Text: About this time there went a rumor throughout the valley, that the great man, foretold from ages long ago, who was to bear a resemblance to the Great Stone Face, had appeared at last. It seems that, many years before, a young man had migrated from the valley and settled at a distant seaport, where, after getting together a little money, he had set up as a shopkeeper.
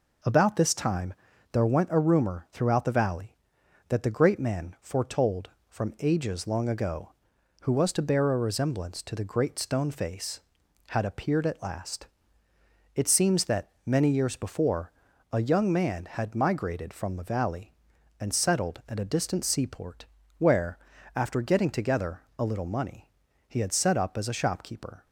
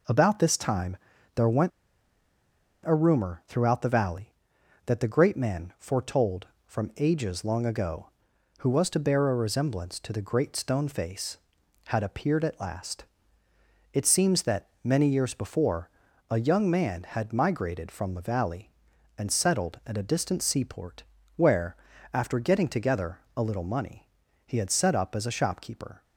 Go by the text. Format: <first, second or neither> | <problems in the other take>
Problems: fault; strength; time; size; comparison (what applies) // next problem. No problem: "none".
first | pauses between "time" and "there"; at 0.9 s; 0.38 s long; also in the first // pauses between "went" and "a"; at 1.7 s; 1.1 s long // pauses between "together" and "a"; slight; at 23.1 s; 0.16 s long; slight in the first